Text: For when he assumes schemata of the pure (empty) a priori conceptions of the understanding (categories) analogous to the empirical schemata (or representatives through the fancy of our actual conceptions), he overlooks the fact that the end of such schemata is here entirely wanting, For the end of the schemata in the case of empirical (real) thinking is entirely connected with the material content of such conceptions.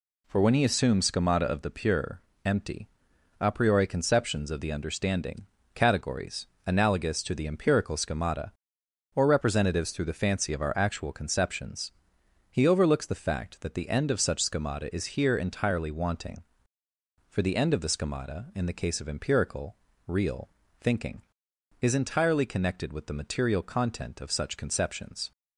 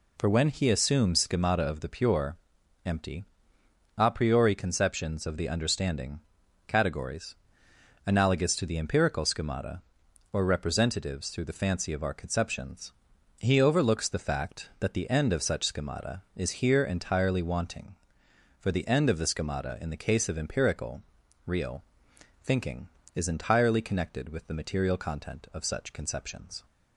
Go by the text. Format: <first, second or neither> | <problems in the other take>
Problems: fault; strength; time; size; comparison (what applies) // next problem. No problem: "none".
first | skips "actual"; at 12.1 s